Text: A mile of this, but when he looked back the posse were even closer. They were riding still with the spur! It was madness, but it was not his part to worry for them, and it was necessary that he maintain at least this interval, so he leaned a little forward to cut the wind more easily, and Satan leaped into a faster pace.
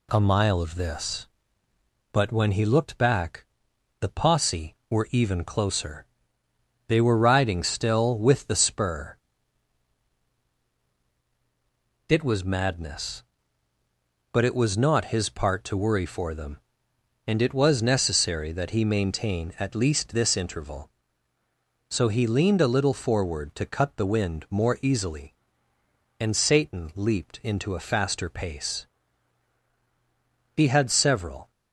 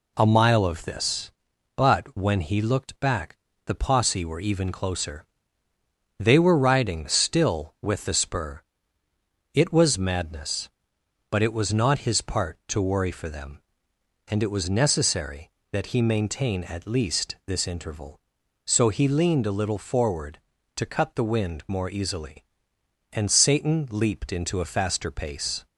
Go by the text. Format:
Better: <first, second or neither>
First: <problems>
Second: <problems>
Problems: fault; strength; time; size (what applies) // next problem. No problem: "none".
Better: second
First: pauses between "back" and "the"; noticeable; at 3.4 s; 0.56 s long // goes on to say "He had several"; noticeable; from 30.5 s on; 0.96 s long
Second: pauses between "back" and "the"; slight; at 3.3 s; 0.30 s long